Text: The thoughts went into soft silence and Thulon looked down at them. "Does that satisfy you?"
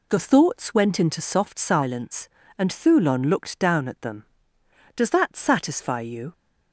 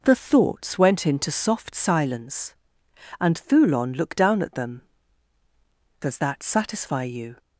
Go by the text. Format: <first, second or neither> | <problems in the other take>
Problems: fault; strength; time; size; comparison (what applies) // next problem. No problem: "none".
neither | none